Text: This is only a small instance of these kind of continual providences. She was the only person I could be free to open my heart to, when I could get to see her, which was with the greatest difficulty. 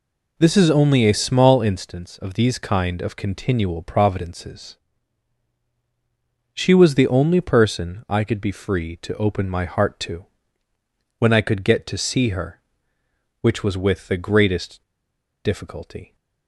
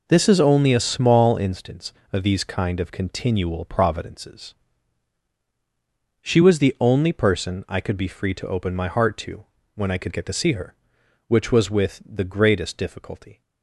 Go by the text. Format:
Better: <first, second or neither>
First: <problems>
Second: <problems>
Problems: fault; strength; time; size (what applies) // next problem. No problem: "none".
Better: second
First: pauses between "greatest" and "difficulty"; noticeable; at 14.8 s; 0.61 s long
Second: none